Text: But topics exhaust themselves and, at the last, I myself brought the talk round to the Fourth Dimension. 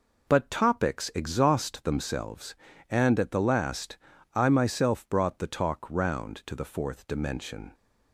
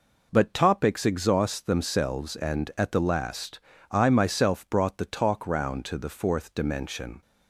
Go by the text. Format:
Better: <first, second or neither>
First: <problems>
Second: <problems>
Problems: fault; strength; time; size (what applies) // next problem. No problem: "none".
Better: neither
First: none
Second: none